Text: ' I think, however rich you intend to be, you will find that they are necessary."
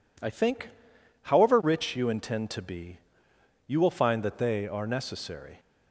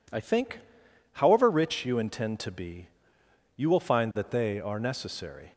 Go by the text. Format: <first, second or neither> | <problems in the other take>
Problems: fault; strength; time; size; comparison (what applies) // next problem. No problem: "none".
neither | none